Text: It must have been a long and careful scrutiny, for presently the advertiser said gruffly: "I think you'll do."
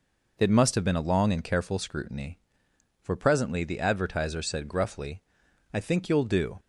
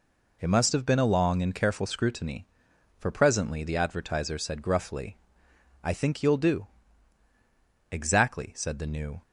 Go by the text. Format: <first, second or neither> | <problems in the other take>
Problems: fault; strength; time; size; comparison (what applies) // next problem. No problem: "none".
first | goes on to say "Exactly said the new"; noticeable; from 7.9 s on; 1.3 s long